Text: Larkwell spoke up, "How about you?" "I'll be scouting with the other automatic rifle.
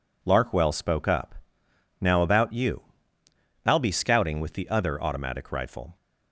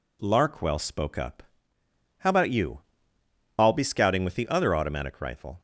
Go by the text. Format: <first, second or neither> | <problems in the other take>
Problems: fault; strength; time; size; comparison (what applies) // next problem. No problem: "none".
second | says "Now" for "How"; at 1.9 s